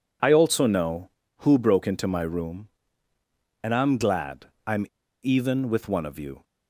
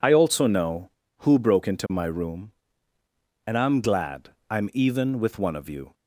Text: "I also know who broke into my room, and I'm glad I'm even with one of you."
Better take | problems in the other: second | pauses between "glad" and "I'm"; slight; at 4.4 s; 0.16 s long; slight in the second // pauses between "I'm" and "even"; at 4.8 s; 0.37 s long

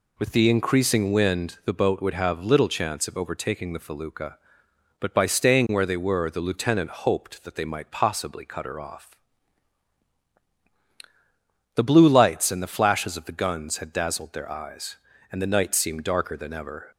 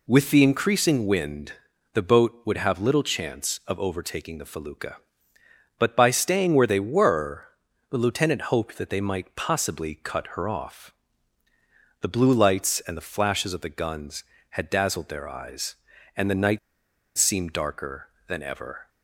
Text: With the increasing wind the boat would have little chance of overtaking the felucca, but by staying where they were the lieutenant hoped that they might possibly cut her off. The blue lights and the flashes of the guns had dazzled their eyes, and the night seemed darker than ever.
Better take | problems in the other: first | pauses between "wind" and "the"; at 1.5 s; 0.42 s long // pauses between "were" and "the"; noticeable; at 7.4 s; 0.46 s long // pauses between "night" and "seemed"; noticeable; at 16.5 s; 0.59 s long

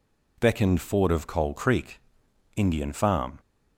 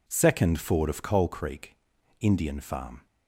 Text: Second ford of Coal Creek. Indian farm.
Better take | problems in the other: second | says "Beckoned" for "Second"; at 0.3 s

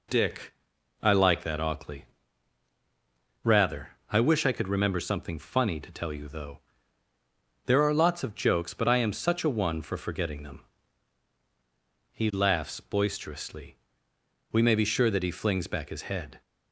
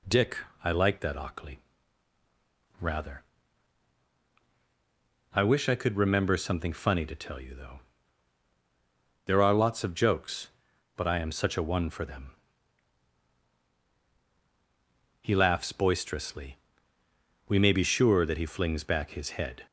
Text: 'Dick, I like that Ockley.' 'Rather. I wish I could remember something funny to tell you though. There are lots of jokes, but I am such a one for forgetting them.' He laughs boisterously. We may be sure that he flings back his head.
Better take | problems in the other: first | skips "forgetting"; at 12.0 s

